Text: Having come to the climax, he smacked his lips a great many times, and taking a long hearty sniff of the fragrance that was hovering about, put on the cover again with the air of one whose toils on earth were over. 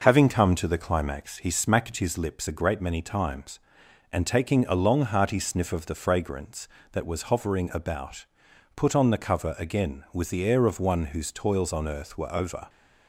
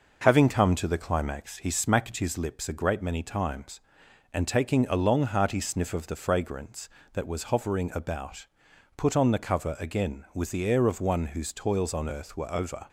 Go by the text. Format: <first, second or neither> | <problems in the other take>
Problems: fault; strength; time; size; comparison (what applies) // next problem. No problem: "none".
neither | none